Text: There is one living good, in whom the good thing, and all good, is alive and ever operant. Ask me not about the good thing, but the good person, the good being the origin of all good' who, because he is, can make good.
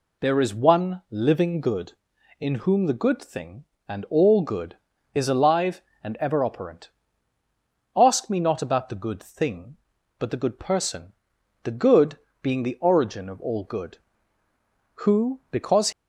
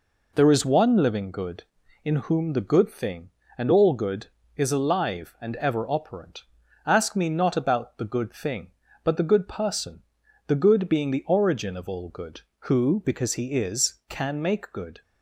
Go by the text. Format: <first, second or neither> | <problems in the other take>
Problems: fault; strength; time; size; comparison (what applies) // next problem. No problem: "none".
second | pauses between "good" and "being"; slight; at 12.1 s; 0.22 s long // stops before "he is can make good"; at 15.9 s